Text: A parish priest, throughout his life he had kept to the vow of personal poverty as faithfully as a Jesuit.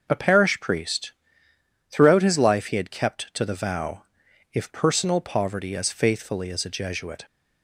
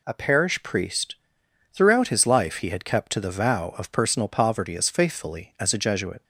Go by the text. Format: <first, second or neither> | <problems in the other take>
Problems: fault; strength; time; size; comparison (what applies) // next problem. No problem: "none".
second | starts louder than the rest; noticeable; until 1.0 s; 6 dB // says "if" for "of"; at 4.5 s